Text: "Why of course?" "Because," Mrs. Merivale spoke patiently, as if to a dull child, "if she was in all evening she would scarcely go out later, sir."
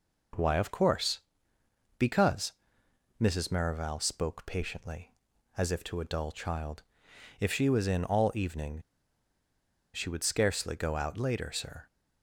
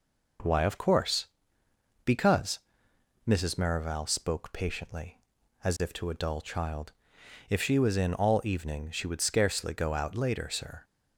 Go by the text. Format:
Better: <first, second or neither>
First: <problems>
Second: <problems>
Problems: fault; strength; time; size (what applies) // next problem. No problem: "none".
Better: second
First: pauses between "evening" and "she"; at 8.8 s; 1.1 s long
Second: none